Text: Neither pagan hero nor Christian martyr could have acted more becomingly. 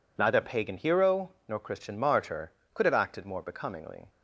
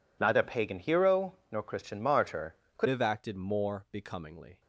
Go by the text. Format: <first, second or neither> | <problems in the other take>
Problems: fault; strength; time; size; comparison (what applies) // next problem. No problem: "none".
first | pauses between "hero" and "nor"; slight; at 1.3 s; 0.16 s long; slight in the first // changes voice at "have"; from 2.8 s on; 1.8 s long